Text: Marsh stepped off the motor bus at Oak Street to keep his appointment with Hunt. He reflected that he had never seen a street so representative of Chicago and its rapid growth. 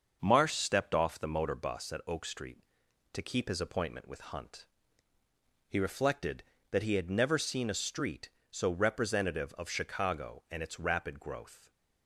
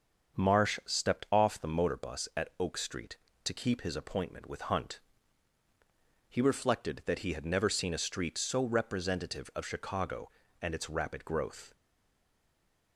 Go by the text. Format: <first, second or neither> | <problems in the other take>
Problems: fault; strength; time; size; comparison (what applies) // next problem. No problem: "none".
first | starts louder than the rest; until 1.4 s; 7 dB; also in the first // stays silent after the last word; noticeable; from 11.7 s on; 1.2 s long